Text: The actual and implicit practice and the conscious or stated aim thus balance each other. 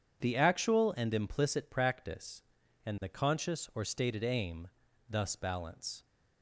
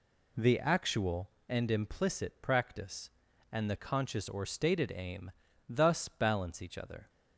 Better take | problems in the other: second | pauses between "aim" and "thus"; at 4.6 s; 0.38 s long; slight in the second // stops before "each other"; at 6.0 s

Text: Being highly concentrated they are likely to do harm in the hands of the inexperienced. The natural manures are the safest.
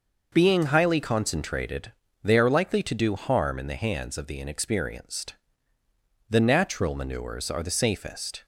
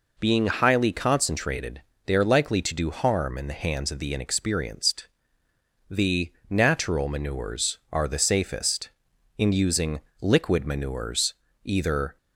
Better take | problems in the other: first | pauses between "concentrated" and "they"; slight; at 1.8 s; 0.26 s long; slight in the first // pauses between "The" and "natural"; slight; at 6.3 s; 0.18 s long // goes on to say "In using liquid manures either"; strong; from 9.3 s on; 2.8 s long

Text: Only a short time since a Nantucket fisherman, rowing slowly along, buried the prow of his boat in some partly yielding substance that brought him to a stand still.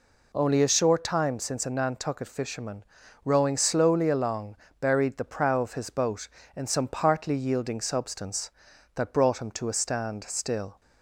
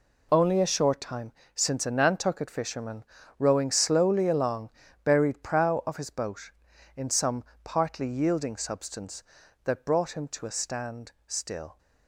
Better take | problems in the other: first | pauses between "time" and "since"; slight; at 1.3 s; 0.24 s long // skips "the"; at 5.4 s // pauses between "some" and "partly"; slight; at 7.4 s; 0.22 s long // pauses between "stand" and "still"; slight; at 11.0 s; 0.16 s long

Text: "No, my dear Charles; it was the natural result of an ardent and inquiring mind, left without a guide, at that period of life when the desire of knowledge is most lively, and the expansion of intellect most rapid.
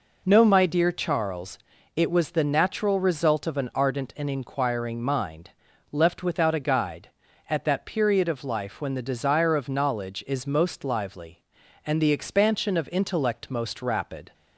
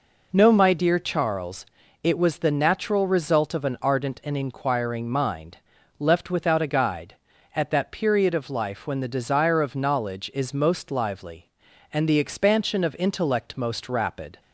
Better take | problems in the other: neither | none

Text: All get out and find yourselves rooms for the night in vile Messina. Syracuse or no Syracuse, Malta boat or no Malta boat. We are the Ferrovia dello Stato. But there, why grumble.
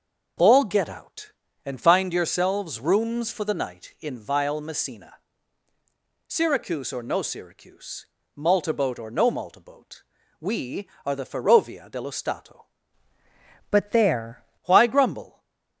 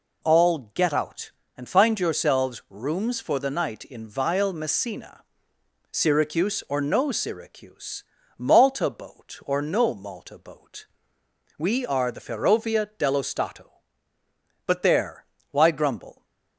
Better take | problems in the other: second | starts louder than the rest; noticeable; until 1.7 s; 6 dB // changes voice from "But" to "there"; from 13.6 to 14.3 s; 0.7 s long // stays silent after the last word; slight; from 15.2 s on; 0.6 s long

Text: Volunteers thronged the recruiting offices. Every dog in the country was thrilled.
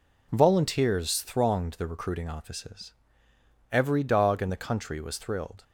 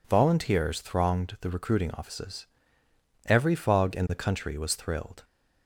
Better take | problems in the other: first | says "fog" for "dog"; at 3.5 s

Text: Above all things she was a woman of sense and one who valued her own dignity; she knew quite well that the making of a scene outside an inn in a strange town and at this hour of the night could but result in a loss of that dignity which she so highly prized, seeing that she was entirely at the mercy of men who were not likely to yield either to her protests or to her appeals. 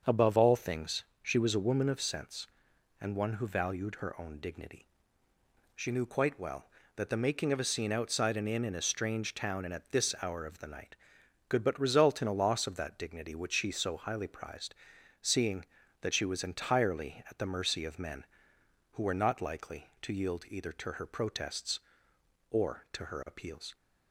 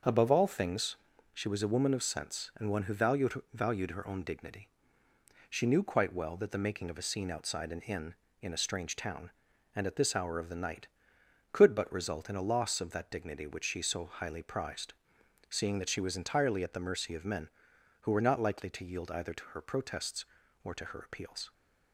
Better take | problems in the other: first | starts louder than the rest; until 1.4 s; 6.5 dB; also in the first // pauses between "things" and "she"; slight; at 0.9 s; 0.36 s long; slight in the first // says "valued" twice; at 3.5 s

